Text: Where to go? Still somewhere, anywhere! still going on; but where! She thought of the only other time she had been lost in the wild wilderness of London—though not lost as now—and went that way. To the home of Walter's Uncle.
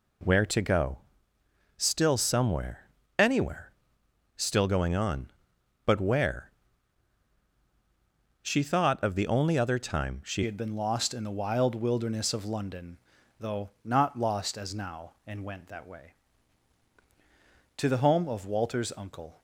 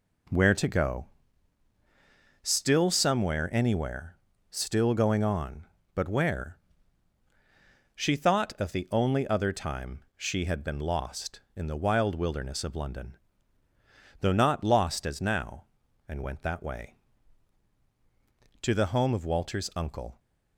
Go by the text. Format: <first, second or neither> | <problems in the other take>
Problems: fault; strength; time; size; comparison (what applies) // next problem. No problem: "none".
second | changes voice at "had"; from 10.4 s on; 9.0 s long